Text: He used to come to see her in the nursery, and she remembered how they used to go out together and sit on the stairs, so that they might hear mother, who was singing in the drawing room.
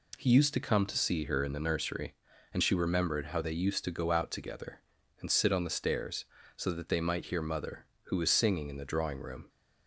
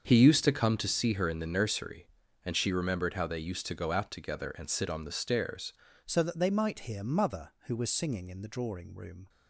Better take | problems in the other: first | starts louder than the rest; until 1.0 s; 6.5 dB // changes voice at "so"; from 6.0 s on; 3.2 s long

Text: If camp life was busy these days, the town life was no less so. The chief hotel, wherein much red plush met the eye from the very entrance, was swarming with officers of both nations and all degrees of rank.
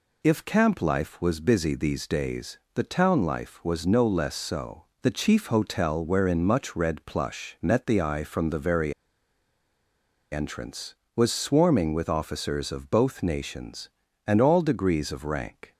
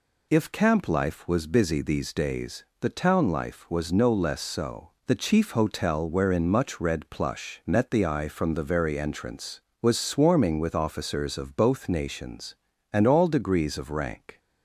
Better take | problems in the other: second | pauses between "very" and "entrance"; strong; at 8.9 s; 1.3 s long

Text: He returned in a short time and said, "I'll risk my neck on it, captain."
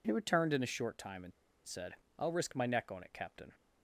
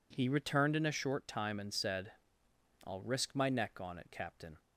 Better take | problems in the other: second | pauses between "and" and "said"; slight; at 1.3 s; 0.34 s long

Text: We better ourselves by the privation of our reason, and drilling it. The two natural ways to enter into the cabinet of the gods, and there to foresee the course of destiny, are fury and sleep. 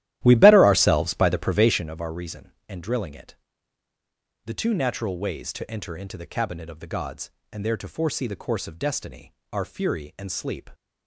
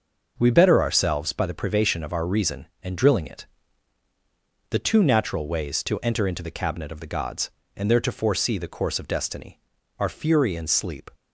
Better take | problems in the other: second | starts louder than the rest; strong; until 1.9 s; 13.5 dB

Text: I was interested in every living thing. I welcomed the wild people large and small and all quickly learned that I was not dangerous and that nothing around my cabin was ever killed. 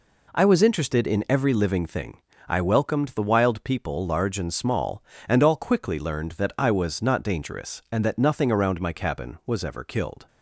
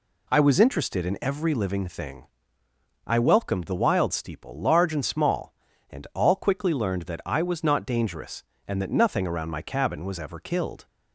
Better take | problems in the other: first | says "steeple" for "people"; at 4.1 s

